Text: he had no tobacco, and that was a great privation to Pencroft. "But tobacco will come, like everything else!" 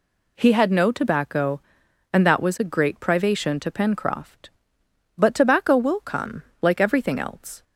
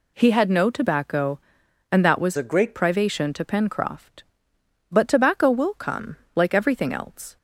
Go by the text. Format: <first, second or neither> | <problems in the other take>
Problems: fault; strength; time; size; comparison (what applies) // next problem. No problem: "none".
first | changes voice from "a" to "great"; from 2.3 to 2.7 s; 0.4 s long